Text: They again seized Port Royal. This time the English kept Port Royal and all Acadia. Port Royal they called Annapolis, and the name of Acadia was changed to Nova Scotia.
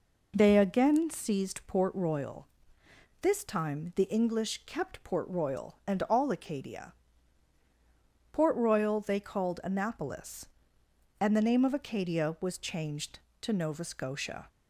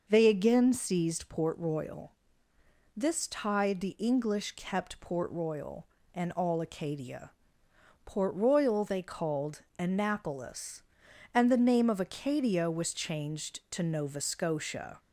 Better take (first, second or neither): first